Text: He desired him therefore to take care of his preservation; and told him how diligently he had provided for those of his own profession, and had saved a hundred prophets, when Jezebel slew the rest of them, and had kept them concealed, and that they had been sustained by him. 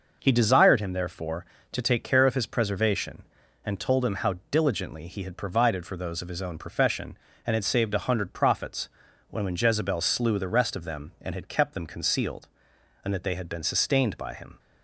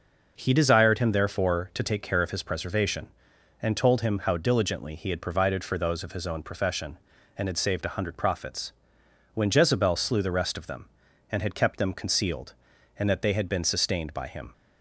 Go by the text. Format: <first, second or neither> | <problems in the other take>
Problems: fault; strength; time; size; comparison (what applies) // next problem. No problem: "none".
second | pauses between "how" and "diligently"; slight; at 4.3 s; 0.16 s long // says "when" twice; at 9.4 s